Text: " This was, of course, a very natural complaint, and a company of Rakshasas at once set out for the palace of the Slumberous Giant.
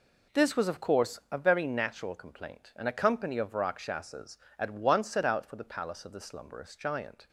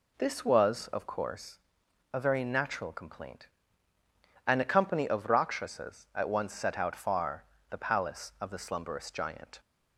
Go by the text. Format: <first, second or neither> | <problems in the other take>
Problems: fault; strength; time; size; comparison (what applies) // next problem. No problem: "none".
first | says "far" for "for"; at 6.9 s